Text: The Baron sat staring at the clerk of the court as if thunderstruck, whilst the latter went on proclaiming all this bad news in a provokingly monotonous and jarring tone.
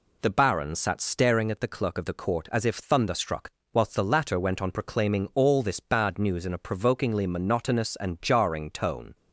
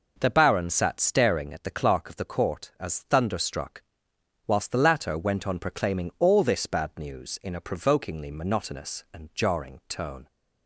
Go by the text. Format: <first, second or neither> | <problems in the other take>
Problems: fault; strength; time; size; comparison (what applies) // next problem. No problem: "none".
first | skips "if"; at 3.0 s